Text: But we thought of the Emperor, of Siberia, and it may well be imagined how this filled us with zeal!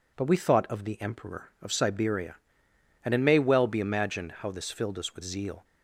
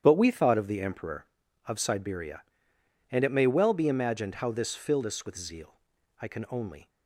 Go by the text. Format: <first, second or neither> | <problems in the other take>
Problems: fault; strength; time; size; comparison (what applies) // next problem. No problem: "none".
first | starts louder than the rest; strong; until 1.0 s; 9.5 dB // goes on to say "I can only"; noticeable; from 6.2 s on; 0.68 s long